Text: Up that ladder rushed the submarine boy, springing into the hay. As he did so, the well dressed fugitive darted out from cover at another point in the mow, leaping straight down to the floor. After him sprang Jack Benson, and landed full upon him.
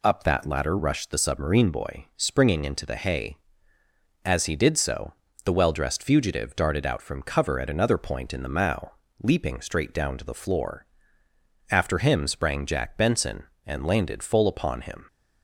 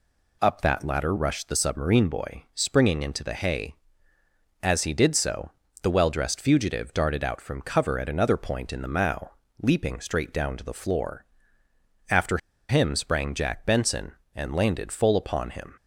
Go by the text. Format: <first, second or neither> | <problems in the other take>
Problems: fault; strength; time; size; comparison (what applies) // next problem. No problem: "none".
first | pauses between "After" and "him"; slight; at 12.3 s; 0.31 s long